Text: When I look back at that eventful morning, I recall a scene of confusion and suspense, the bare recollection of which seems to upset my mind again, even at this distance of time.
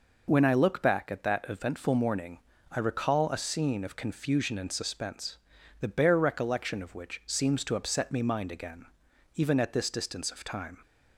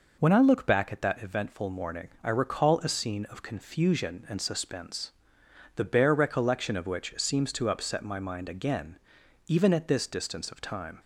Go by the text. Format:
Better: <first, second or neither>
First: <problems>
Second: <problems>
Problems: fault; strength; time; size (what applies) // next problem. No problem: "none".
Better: second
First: says "me" for "my"; at 8.1 s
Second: none